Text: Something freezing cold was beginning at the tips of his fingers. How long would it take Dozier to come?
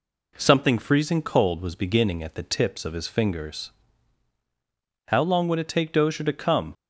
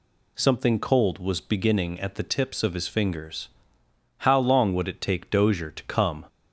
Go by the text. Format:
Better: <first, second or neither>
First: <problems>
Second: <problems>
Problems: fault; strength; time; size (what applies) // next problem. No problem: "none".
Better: first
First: none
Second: skips "freezing"; at 0.7 s